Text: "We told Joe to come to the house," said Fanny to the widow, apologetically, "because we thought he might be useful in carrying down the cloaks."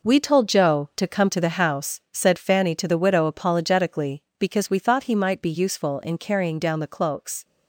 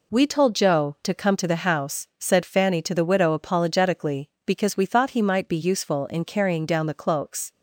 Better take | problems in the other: second | gets quieter; strong; throughout; 9.5 dB

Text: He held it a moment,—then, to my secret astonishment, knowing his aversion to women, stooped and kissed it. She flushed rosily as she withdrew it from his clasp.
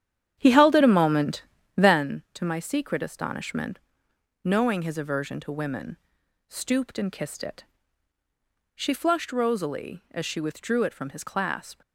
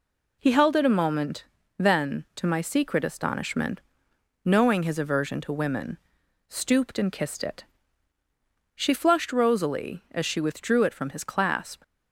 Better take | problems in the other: second | starts louder than the rest; strong; until 2.2 s; 10 dB

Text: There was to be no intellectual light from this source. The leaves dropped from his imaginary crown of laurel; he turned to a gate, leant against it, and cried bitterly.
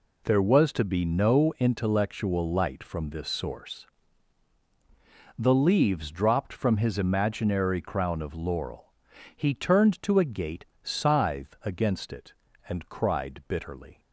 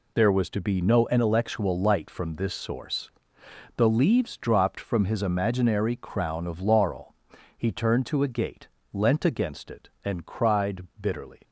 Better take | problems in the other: second | says "scythe" for "leant"; at 10.8 s

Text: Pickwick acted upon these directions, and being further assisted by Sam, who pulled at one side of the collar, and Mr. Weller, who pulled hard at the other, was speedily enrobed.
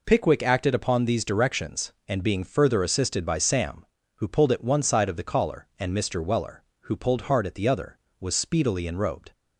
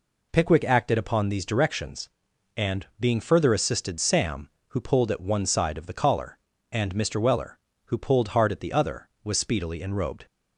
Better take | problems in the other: first | skips "by"; at 3.9 s

